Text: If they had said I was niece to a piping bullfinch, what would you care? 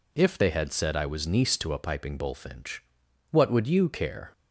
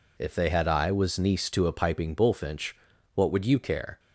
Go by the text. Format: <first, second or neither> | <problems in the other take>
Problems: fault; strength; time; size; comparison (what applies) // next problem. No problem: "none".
first | skips "said"; at 0.6 s